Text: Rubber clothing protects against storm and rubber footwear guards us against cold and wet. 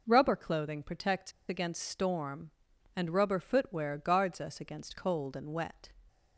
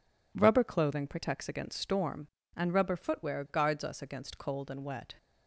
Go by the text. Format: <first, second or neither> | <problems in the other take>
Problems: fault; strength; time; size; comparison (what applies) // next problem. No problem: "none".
second | pauses between "protects" and "against"; slight; at 1.3 s; 0.17 s long